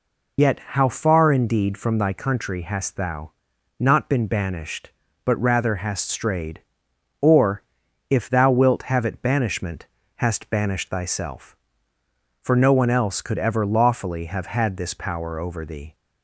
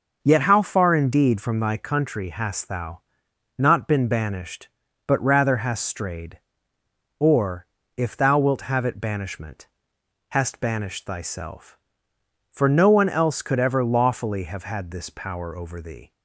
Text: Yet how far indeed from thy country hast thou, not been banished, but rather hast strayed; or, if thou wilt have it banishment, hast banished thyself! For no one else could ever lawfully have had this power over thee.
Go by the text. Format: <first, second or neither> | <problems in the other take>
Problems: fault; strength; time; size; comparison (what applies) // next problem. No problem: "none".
second | loses the start of "Yet"; at 0.3 s; 65 ms